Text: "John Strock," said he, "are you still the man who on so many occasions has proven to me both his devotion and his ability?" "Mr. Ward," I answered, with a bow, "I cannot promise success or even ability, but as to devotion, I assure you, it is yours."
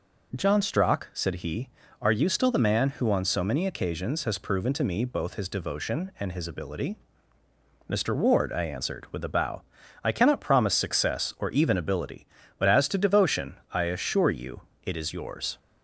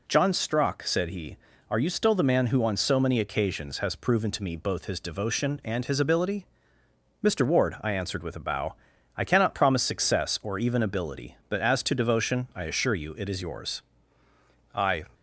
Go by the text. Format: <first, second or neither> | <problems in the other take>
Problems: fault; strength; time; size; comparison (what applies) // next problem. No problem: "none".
first | goes on to say "I"; slight; from 14.7 s on; 0.30 s long